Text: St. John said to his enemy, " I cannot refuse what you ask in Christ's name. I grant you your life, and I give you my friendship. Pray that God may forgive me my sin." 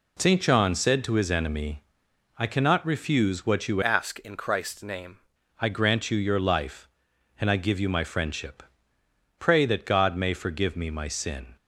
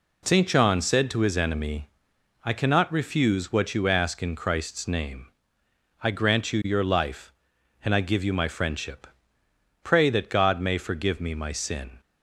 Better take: second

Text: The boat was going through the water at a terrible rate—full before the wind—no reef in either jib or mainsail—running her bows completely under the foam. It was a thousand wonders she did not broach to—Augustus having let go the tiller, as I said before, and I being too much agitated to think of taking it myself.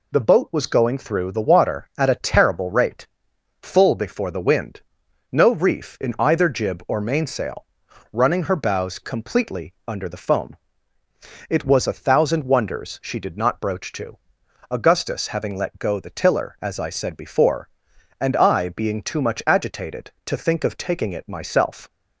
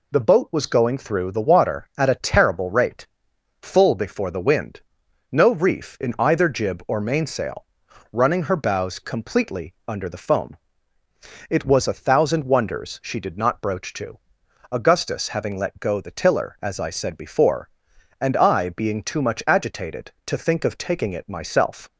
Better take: neither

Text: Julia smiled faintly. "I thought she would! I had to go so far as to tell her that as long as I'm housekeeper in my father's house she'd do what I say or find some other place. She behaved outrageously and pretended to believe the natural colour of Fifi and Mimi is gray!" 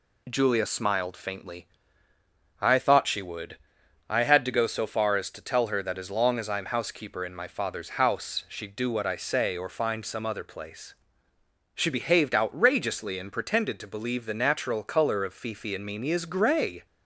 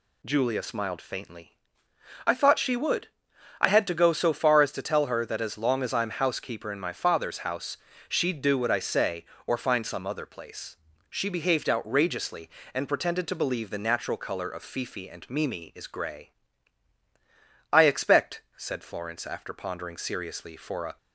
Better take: first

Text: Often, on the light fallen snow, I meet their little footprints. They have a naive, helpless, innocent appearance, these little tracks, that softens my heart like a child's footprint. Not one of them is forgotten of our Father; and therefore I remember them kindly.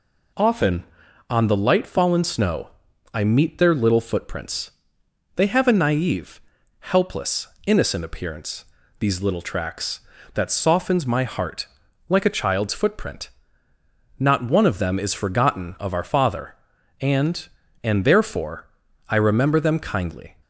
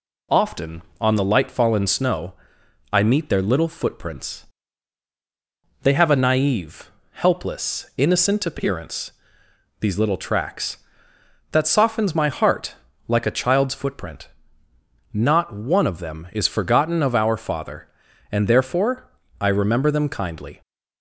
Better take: second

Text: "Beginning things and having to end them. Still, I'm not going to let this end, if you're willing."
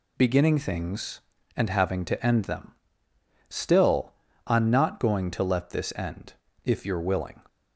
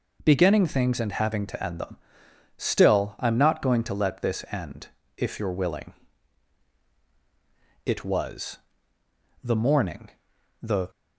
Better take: first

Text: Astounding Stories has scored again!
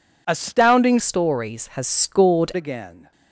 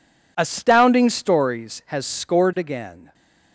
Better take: second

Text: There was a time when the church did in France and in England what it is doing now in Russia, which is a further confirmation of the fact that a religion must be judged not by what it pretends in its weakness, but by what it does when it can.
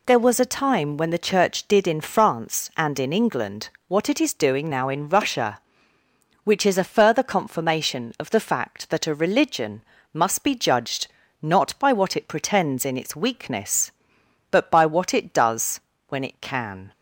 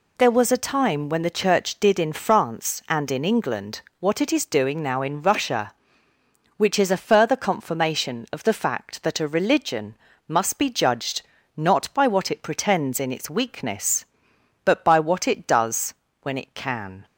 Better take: neither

